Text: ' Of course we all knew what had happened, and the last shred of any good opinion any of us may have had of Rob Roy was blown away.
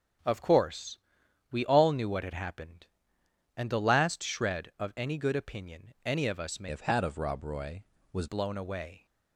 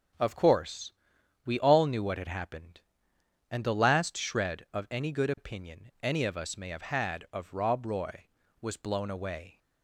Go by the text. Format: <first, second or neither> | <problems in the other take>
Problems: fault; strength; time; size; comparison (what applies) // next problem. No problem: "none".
second | starts louder than the rest; noticeable; until 1.7 s; 6 dB // pauses between "course" and "we"; noticeable; at 0.9 s; 0.52 s long; noticeable in the second // changes voice from "have" to "was"; from 6.6 to 8.2 s; 1.6 s long